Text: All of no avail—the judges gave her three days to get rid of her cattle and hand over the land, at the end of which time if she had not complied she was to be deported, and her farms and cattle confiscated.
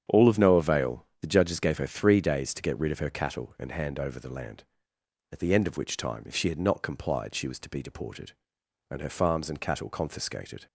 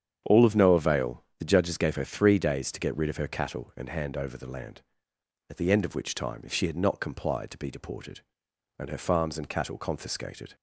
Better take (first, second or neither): first